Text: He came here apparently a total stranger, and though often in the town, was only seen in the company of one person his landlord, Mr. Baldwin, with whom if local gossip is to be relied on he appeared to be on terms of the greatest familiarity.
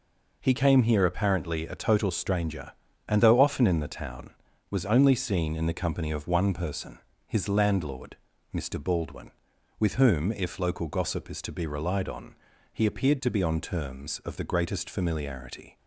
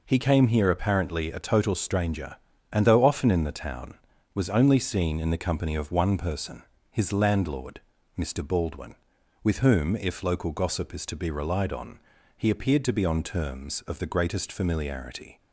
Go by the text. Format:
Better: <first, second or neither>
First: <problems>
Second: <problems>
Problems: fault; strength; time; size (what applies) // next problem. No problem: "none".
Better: neither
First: pauses between "person" and "his"; slight; at 6.9 s; 0.28 s long // pauses between "on" and "he"; slight; at 12.3 s; 0.36 s long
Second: pauses between "person" and "his"; slight; at 6.6 s; 0.28 s long // pauses between "on" and "he"; slight; at 11.9 s; 0.36 s long